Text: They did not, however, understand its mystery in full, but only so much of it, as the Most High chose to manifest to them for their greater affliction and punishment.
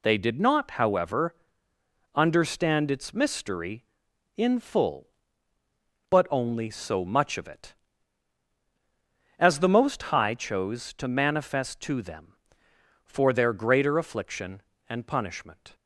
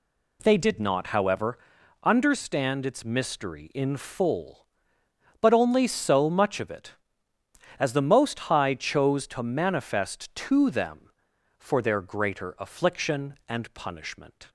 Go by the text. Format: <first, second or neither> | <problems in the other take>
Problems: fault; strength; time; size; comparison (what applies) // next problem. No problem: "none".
neither | none